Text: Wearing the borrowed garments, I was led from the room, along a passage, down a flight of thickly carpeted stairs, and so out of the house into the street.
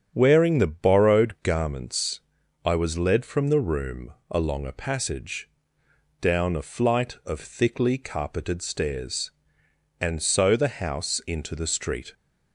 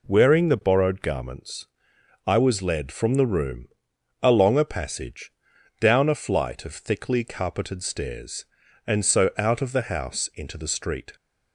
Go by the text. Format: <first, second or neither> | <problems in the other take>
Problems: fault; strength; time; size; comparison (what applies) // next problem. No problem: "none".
second | starts louder than the rest; strong; until 1.1 s; 7.5 dB // skips "out of"; at 10.5 s